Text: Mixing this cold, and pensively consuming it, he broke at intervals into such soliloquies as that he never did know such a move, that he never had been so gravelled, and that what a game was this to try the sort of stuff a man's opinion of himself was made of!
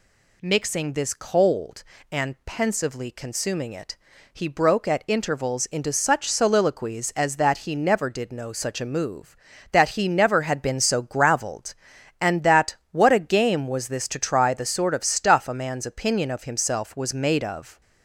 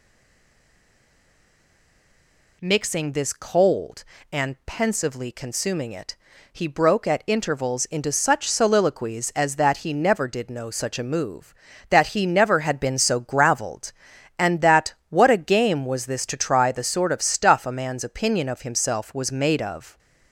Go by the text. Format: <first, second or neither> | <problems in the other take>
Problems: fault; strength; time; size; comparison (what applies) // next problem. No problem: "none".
first | stays silent before the first word; strong; until 2.6 s; 2.6 s long // pauses between "that" and "what"; slight; at 14.9 s; 0.16 s long; slight in the first